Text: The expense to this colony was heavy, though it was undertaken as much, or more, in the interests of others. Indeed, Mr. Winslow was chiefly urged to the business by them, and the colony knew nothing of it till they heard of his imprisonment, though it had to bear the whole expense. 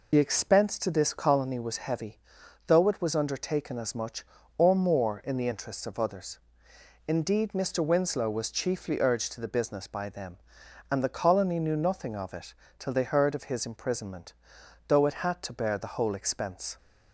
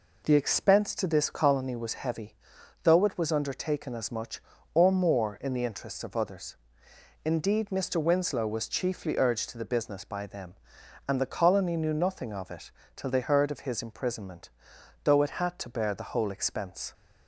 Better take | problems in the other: second | loses the start of "The"; at 0.1 s; 45 ms // pauses between "it" and "till"; slight; at 12.5 s; 0.26 s long; slight in the second

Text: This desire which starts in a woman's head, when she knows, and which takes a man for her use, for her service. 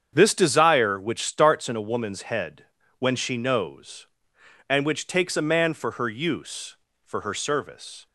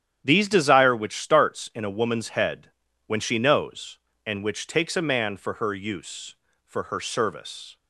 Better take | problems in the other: first | starts louder than the rest; strong; until 1.2 s; 9.5 dB; strong in the first // says "These" for "This"; at 0.2 s

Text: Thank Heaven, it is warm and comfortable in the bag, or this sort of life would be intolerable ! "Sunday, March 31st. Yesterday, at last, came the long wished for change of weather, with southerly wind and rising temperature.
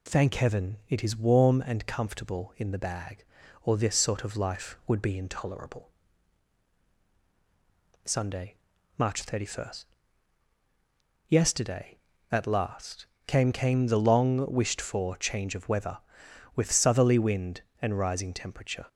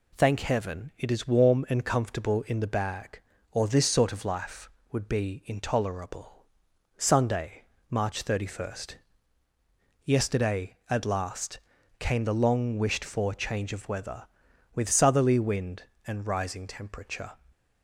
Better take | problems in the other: second | says "came" twice; at 13.5 s

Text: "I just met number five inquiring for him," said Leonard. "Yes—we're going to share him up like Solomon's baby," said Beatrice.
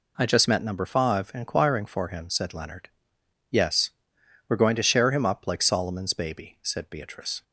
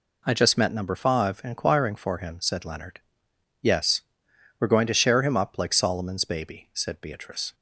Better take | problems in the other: neither | none

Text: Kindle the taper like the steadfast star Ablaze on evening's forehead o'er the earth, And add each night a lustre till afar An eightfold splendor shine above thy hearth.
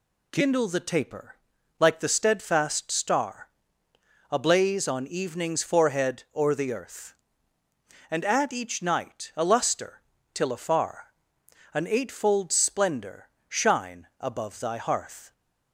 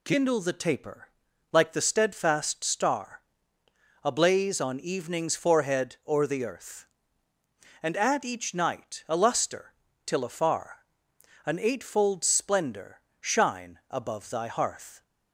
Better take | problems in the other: neither | pauses between "taper" and "like"; the same in both // pauses between "star" and "Ablaze"; noticeable; the same in both // pauses between "lustre" and "till"; slight; the same in both // pauses between "afar" and "An"; noticeable; the same in both // pauses between "splendor" and "shine"; slight; the same in both

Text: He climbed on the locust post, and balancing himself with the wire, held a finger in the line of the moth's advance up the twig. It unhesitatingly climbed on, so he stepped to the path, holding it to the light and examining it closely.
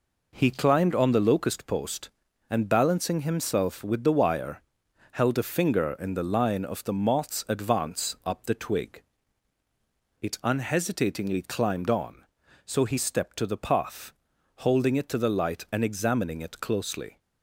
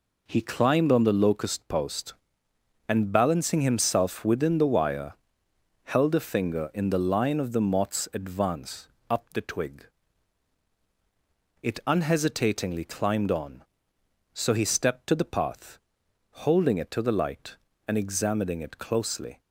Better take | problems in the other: first | says "within" for "with"; at 4.2 s // pauses between "advance" and "up"; slight; at 8.8 s; 0.20 s long

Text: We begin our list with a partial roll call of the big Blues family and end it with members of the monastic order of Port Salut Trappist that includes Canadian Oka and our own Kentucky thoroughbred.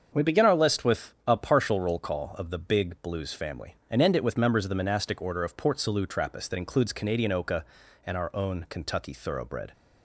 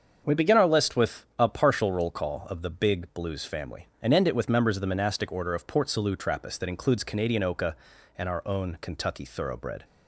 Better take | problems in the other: neither | starts louder than the rest; the same in both

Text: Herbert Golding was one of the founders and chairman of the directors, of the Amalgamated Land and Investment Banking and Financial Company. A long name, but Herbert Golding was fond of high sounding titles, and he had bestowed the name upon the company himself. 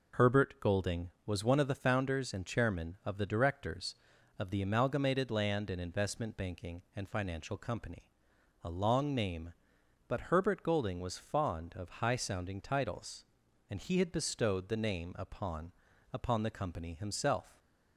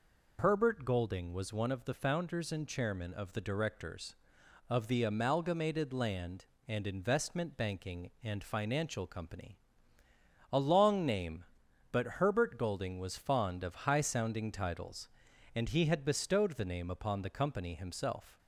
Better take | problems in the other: second | says "upon" twice; at 16.1 s

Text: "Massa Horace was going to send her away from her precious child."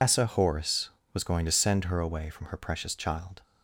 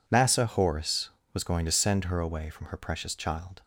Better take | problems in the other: second | loses the start of "Massa"; at 0.0 s; 130 ms

